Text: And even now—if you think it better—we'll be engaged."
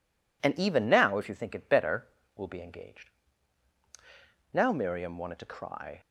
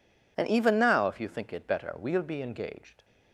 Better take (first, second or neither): second